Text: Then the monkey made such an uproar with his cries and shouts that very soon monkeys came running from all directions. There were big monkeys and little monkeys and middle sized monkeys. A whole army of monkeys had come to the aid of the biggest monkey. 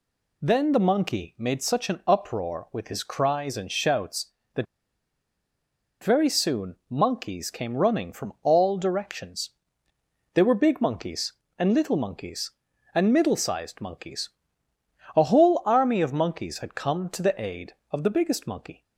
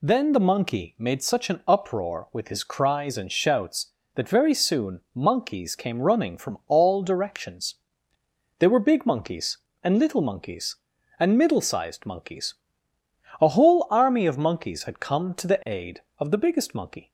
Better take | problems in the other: second | pauses between "that" and "very"; strong; at 4.6 s; 1.3 s long

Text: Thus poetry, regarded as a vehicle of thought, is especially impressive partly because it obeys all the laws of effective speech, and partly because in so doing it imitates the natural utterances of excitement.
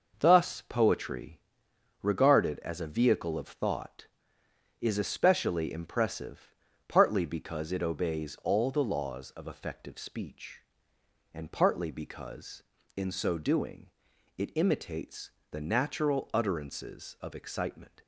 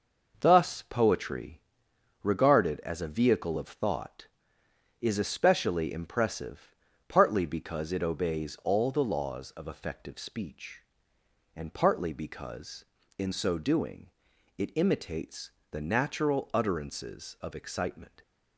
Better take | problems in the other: neither | pauses between "impressive" and "partly"; slight; the same in both // pauses between "doing" and "it"; noticeable; the same in both // pauses between "imitates" and "the"; slight; the same in both

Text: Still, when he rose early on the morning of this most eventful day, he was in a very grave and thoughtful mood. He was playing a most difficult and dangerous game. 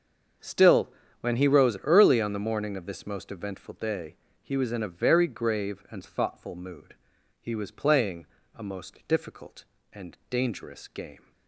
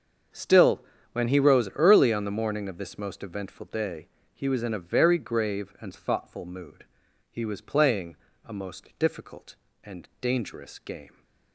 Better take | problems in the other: neither | starts louder than the rest; the same in both // pauses between "playing" and "a"; slight; the same in both

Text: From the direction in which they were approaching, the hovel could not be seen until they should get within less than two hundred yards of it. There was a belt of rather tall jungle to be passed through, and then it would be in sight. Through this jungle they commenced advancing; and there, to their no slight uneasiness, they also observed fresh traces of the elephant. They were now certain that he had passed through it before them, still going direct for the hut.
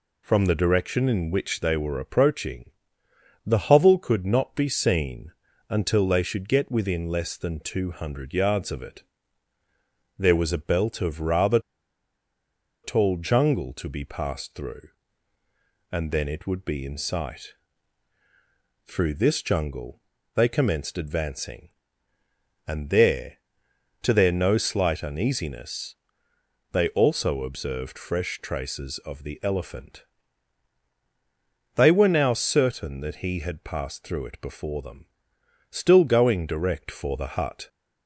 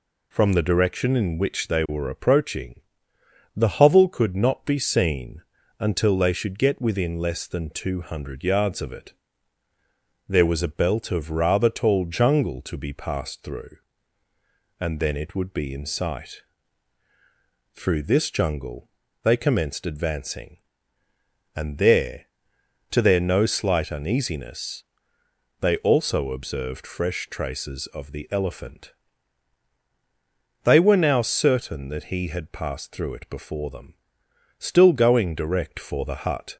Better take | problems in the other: second | pauses between "seen" and "until"; slight; at 5.3 s; 0.36 s long; slight in the second // pauses between "rather" and "tall"; at 11.6 s; 1.2 s long // pauses between "jungle" and "they"; slight; at 19.9 s; 0.34 s long; slight in the second

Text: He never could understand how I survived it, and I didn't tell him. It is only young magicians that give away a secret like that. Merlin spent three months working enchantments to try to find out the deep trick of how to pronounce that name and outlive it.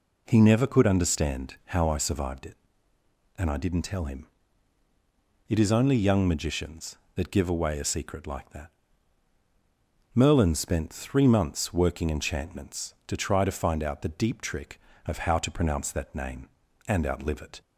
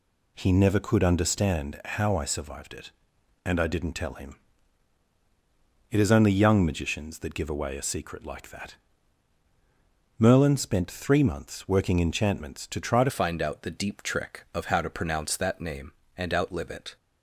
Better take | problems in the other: first | changes voice at "find"; from 13.0 s on; 3.9 s long

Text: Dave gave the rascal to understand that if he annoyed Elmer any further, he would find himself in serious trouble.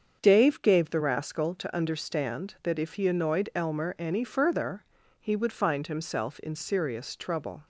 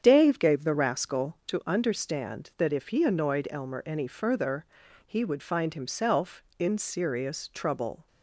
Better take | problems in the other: neither | starts louder than the rest; the same in both

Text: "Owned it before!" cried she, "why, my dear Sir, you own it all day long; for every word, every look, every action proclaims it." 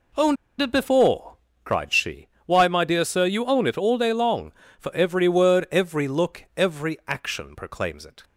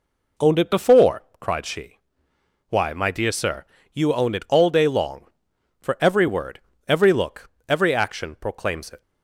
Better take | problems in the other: second | pauses between "Owned" and "it"; slight; at 0.3 s; 0.24 s long

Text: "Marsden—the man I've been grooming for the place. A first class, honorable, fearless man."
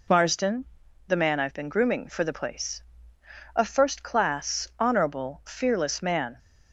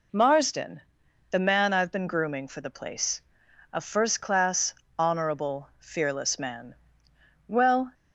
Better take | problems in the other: first | goes on to say "Well"; slight; from 7.4 s on; 0.48 s long

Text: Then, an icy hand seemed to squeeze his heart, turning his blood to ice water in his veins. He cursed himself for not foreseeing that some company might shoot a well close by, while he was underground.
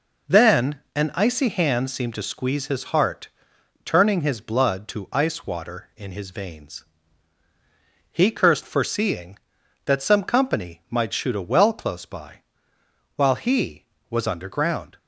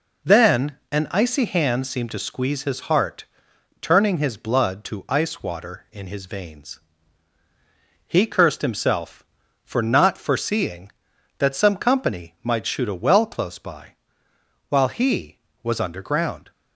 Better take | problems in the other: second | skips "himself for not"; at 8.6 s

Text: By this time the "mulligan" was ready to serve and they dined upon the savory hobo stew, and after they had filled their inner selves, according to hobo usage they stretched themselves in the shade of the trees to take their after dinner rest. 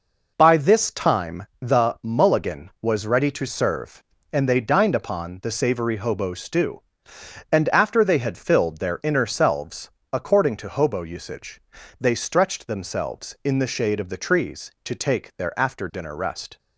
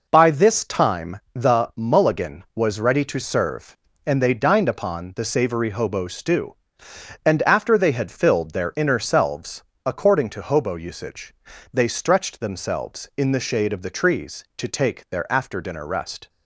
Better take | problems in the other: neither | pauses between "usage" and "they"; the same in both

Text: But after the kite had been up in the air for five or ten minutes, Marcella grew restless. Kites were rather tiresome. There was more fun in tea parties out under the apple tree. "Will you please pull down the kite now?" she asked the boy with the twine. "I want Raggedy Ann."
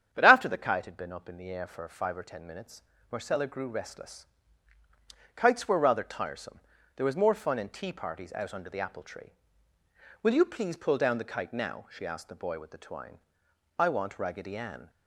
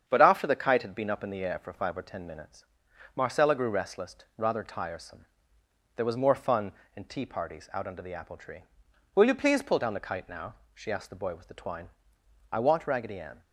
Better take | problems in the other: first | starts louder than the rest; strong; until 1.0 s; 8 dB; strong in the first // skips "Kites were"; at 4.2 s

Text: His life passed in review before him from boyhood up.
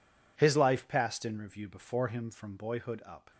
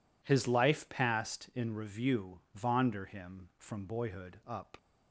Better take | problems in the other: first | says "vonder" for "before"; at 2.5 s

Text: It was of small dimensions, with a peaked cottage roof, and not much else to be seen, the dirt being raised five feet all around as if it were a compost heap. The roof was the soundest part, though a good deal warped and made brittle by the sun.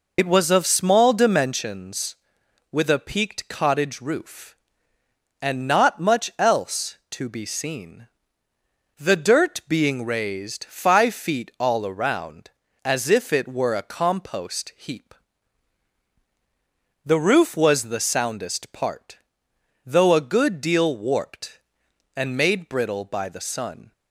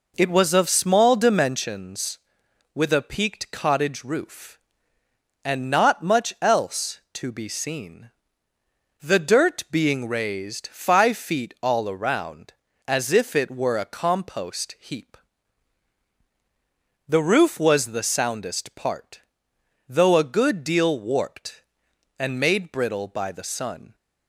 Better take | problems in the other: second | loses the start of "It"; at 0.1 s; 55 ms

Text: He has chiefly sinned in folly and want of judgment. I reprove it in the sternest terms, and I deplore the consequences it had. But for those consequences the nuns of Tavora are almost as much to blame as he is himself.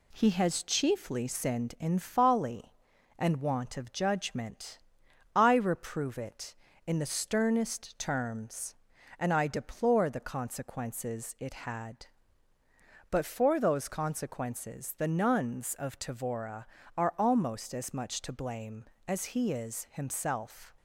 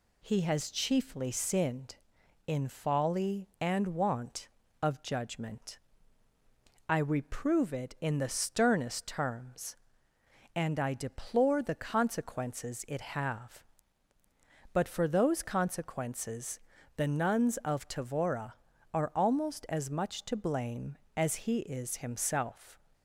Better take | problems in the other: first | says "have" for "had"; at 13.0 s // pauses between "consequences" and "the"; slight; at 16.6 s; 0.34 s long

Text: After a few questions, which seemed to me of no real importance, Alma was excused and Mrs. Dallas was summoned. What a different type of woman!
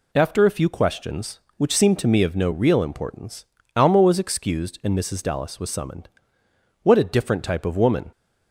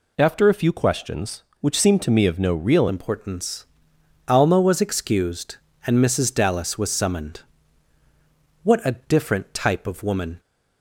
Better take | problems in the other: first | changes voice at "importance"; from 2.8 s on; 7.5 s long

